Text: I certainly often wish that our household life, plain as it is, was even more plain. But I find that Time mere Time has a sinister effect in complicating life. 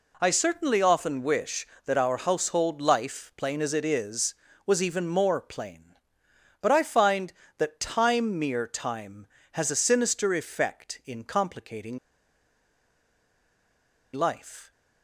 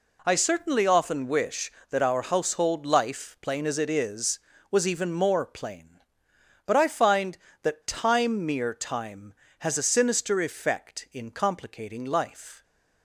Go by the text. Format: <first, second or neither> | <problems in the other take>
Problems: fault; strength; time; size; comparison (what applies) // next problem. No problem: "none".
second | pauses between "complicating" and "life"; strong; at 11.9 s; 2.1 s long